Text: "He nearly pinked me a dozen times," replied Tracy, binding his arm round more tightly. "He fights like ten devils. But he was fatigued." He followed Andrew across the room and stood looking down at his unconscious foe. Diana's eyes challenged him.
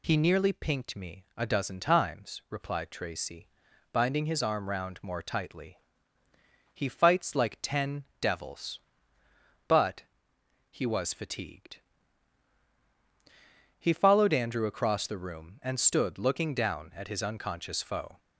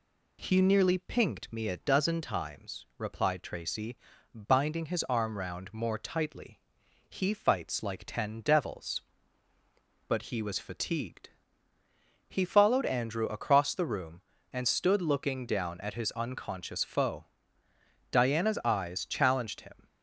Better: second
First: pauses between "ten" and "devils"; slight; at 8.0 s; 0.16 s long // pauses between "But" and "he"; noticeable; at 10.0 s; 0.66 s long // stops before "Diana's eyes challenged him"; at 18.1 s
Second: none

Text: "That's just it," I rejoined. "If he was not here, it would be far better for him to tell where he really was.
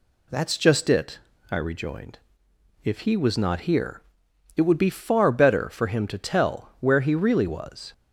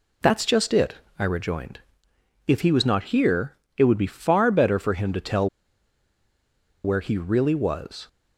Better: first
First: none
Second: pauses between "tell" and "where"; strong; at 5.4 s; 1.3 s long

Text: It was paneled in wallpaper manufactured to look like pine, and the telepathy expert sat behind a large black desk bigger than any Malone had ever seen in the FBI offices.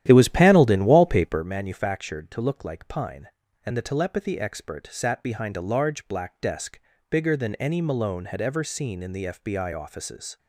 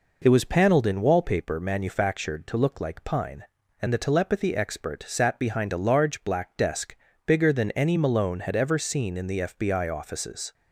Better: second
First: starts louder than the rest; strong; until 1.5 s; 11.5 dB // pauses between "desk" and "bigger"; slight; at 6.7 s; 0.32 s long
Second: pauses between "desk" and "bigger"; slight; at 6.9 s; 0.32 s long

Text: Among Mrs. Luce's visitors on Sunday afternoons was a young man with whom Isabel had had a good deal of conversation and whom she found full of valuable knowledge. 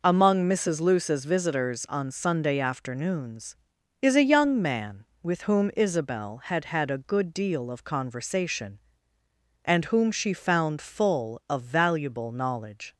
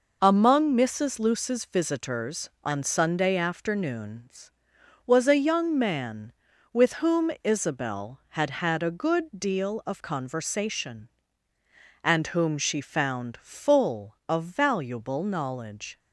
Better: second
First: says "is" for "was"; at 3.9 s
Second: none

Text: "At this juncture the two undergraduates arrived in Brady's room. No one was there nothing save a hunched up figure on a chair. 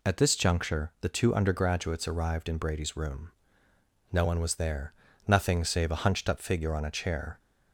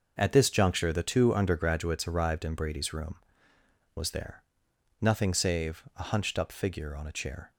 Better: first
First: pauses between "there" and "nothing"; slight; at 4.9 s; 0.34 s long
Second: skips "No one"; at 3.5 s // pauses between "there" and "nothing"; noticeable; at 4.4 s; 0.60 s long

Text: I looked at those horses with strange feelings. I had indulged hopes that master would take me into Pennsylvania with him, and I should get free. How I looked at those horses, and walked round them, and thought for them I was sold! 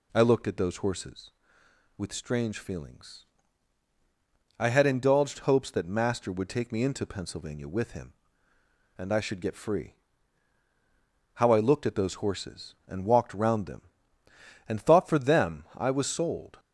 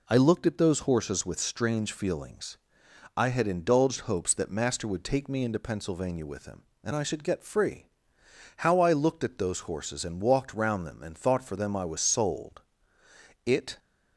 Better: first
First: none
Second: goes on to say "It"; slight; from 13.4 s on; 0.34 s long

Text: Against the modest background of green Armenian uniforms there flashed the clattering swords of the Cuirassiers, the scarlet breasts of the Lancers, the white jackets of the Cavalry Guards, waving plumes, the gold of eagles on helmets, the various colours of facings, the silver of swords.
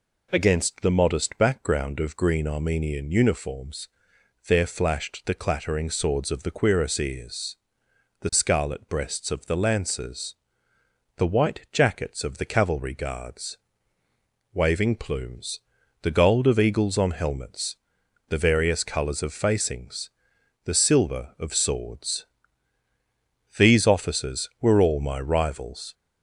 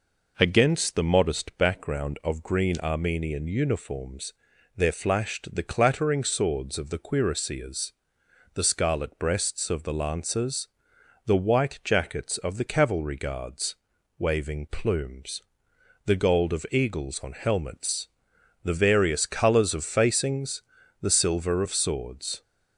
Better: second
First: pauses between "uniforms" and "there"; noticeable; at 3.8 s; 0.58 s long // goes on to say "These officers were all my rivals"; strong; from 23.5 s on; 2.3 s long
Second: pauses between "uniforms" and "there"; at 4.3 s; 0.42 s long

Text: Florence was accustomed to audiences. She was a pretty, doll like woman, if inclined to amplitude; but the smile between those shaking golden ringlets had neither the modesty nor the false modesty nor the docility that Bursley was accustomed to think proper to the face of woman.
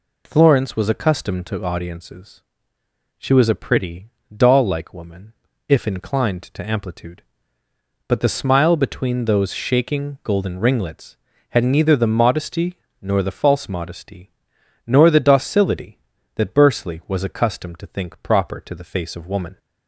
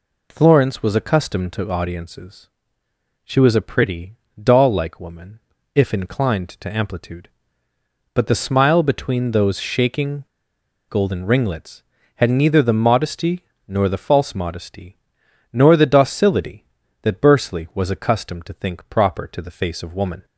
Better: first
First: pauses between "modesty" and "nor"; slight; at 12.7 s; 0.24 s long // pauses between "modesty" and "nor"; noticeable; at 14.3 s; 0.56 s long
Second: pauses between "shaking" and "golden"; noticeable; at 10.2 s; 0.65 s long // pauses between "modesty" and "nor"; slight; at 13.4 s; 0.24 s long // pauses between "modesty" and "nor"; noticeable; at 14.9 s; 0.56 s long

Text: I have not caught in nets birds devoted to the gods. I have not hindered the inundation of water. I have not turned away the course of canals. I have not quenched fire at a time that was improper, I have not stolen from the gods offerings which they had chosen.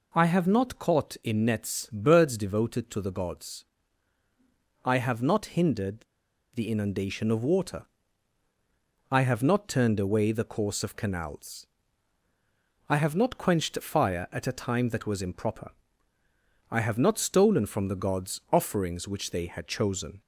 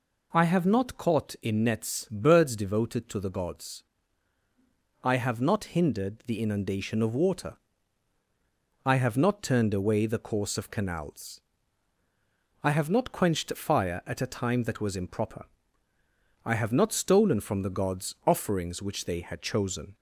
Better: second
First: pauses between "hindered" and "the"; noticeable; at 6.0 s; 0.51 s long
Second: none

